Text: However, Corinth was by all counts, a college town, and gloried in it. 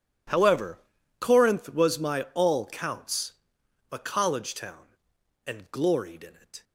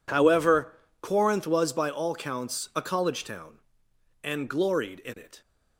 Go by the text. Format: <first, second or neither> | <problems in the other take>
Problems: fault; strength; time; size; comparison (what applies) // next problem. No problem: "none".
second | says "my" for "by"; at 1.9 s